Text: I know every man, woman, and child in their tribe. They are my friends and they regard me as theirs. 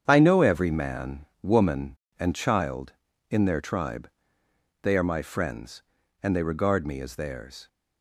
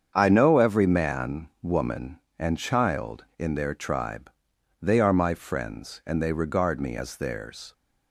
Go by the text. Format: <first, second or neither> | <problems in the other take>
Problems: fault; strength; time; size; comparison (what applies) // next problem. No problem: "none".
neither | starts louder than the rest; strong; the same in both